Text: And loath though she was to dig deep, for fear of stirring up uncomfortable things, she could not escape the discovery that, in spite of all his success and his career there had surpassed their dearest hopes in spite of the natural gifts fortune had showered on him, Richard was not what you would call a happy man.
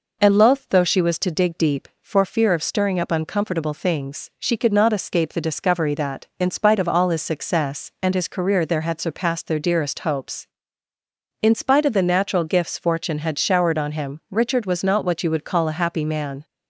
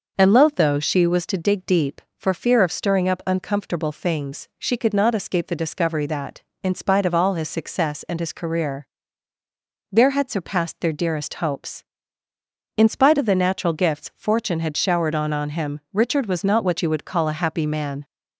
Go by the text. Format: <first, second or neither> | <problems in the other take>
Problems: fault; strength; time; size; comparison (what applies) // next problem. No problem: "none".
first | pauses between "career" and "there"; at 8.8 s; 1.0 s long // says "on" twice; at 15.3 s